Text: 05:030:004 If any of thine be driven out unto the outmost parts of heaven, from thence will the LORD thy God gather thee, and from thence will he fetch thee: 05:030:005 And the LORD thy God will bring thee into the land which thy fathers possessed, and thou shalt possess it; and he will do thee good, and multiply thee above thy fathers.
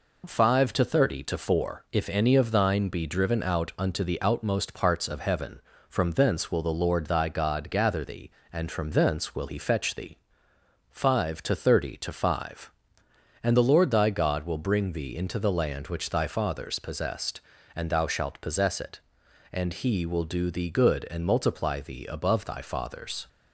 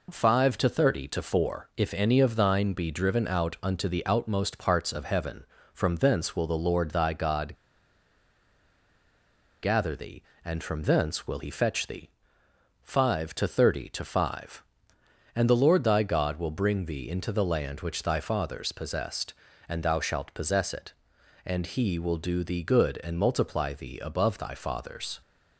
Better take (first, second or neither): first